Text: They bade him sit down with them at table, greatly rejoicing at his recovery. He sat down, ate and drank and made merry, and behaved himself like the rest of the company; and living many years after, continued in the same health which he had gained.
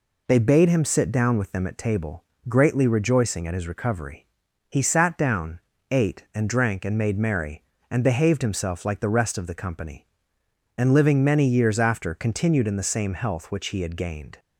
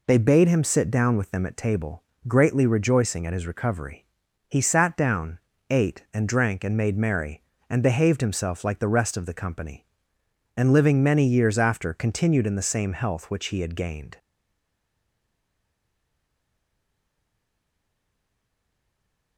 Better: first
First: none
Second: stays silent after the last word; strong; from 14.1 s on; 5.2 s long

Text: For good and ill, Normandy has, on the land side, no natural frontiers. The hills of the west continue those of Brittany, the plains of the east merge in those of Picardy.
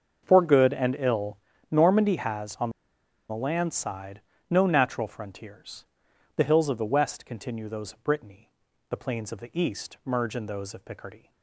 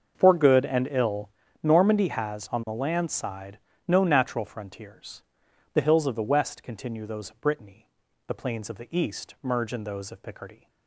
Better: second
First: starts louder than the rest; until 1.2 s; 6.5 dB // pauses between "on" and "the"; noticeable; at 2.7 s; 0.59 s long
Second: starts louder than the rest; until 1.1 s; 6.5 dB

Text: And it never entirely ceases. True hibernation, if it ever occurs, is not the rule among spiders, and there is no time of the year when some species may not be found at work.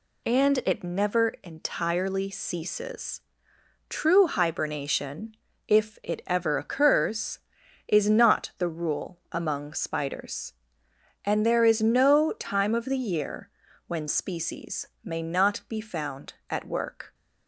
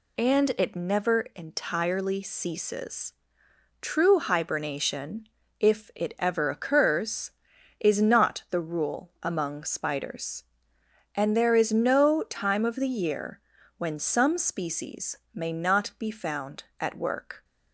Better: second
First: pauses between "year" and "when"; at 13.4 s; 0.38 s long // skips "some"; at 14.0 s // pauses between "species" and "may"; slight; at 14.8 s; 0.18 s long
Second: pauses between "year" and "when"; at 13.3 s; 0.38 s long // pauses between "species" and "may"; slight; at 15.1 s; 0.18 s long

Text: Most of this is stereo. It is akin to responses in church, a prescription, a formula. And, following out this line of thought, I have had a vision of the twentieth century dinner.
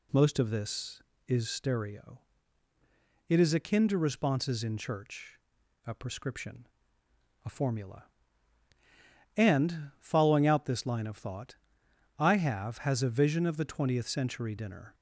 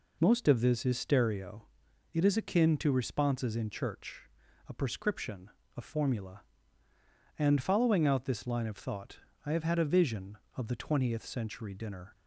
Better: second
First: says "has" for "had"; at 12.7 s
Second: none

